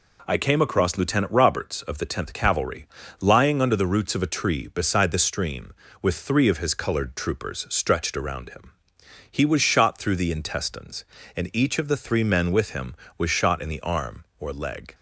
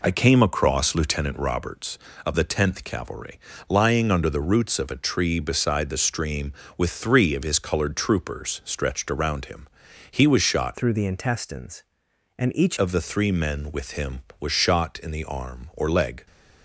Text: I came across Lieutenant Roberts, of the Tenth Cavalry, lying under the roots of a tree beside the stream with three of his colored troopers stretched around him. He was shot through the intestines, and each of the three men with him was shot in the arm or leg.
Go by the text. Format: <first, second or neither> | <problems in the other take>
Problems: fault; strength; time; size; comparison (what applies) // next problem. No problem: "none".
first | changes voice from "through" to "each"; from 10.7 to 12.7 s; 2.0 s long